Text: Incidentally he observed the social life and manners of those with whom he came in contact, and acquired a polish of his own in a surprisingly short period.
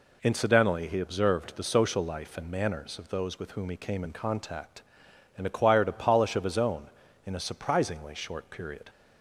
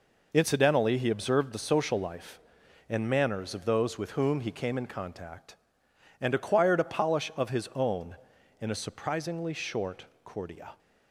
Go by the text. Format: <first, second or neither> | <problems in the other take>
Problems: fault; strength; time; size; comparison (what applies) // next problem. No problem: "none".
first | says "cordia" for "period"; at 10.2 s